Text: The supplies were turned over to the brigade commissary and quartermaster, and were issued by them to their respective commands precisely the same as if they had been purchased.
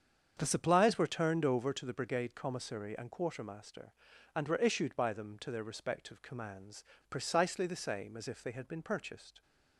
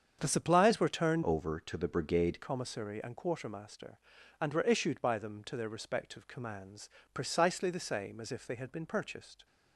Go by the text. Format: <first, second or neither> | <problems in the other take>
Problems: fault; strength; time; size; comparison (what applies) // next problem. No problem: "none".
first | starts louder than the rest; strong; until 1.2 s; 7.5 dB; strong in the first // changes voice from "over" to "brigade"; from 1.2 to 2.3 s; 1.1 s long // pauses between "commands" and "precisely"; slight; at 6.8 s; 0.24 s long; slight in the first